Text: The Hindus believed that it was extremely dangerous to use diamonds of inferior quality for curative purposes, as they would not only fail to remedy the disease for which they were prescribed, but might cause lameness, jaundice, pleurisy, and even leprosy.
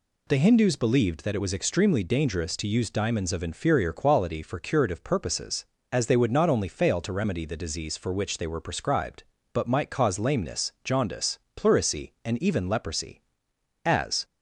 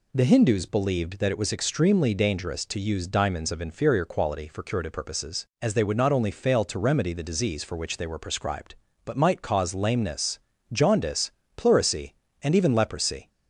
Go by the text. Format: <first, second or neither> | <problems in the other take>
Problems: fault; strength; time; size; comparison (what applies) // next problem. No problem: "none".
second | goes on to say "As"; slight; from 13.8 s on; 0.40 s long